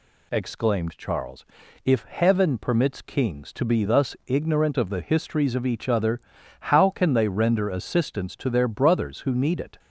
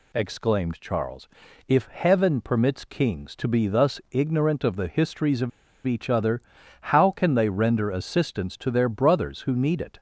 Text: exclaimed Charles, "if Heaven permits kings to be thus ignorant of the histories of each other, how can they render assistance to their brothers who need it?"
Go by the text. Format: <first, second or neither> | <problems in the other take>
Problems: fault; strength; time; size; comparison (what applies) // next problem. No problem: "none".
first | pauses between "of" and "each"; at 5.4 s; 0.37 s long